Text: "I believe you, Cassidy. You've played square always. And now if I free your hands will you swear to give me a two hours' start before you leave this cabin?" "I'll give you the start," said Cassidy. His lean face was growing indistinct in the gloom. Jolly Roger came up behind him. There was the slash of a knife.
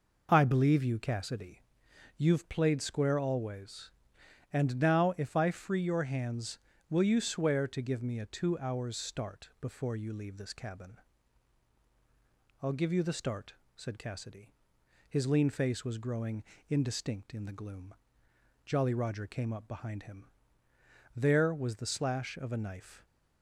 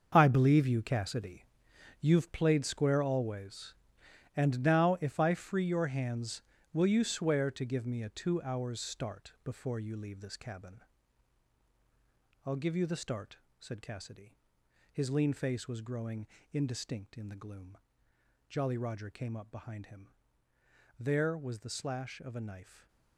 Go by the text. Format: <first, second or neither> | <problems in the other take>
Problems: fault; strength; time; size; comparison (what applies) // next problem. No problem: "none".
first | gets quieter; strong; throughout; 12.5 dB // pauses between "growing" and "indistinct"; slight; at 16.2 s; 0.24 s long; slight in the first